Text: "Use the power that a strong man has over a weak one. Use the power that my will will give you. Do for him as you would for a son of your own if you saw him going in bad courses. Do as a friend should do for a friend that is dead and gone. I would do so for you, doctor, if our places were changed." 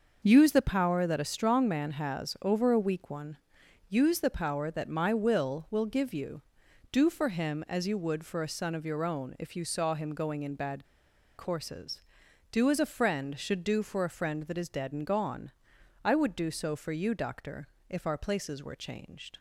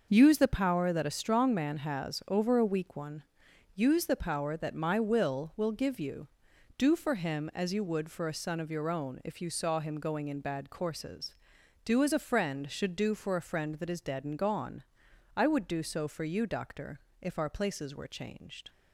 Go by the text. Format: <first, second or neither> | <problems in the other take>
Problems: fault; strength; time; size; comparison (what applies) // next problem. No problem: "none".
second | starts louder than the rest; noticeable; until 1.2 s; 6 dB; noticeable in the second // pauses between "bad" and "courses"; noticeable; at 10.8 s; 0.53 s long